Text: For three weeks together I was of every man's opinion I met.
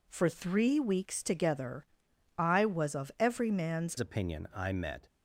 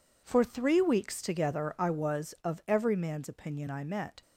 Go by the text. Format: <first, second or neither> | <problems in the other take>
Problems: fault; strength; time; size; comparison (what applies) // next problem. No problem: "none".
second | pauses between "together" and "I"; noticeable; at 1.8 s; 0.52 s long // changes voice at "opinion"; from 3.9 s on; 1.1 s long